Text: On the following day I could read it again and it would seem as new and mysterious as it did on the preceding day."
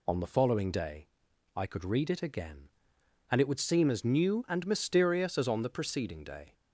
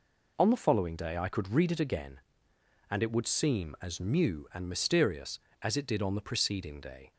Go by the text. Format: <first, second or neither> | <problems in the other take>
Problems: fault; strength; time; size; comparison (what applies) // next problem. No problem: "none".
second | pauses between "day" and "I"; noticeable; at 1.0 s; 0.48 s long // skips "it did"; at 5.4 s